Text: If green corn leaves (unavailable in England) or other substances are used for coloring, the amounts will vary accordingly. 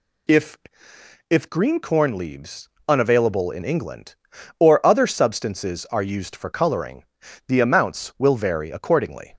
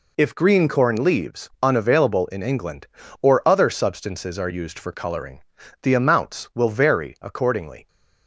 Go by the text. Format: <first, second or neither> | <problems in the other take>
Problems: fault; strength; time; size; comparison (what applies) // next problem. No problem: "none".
second | says "If" twice; at 1.2 s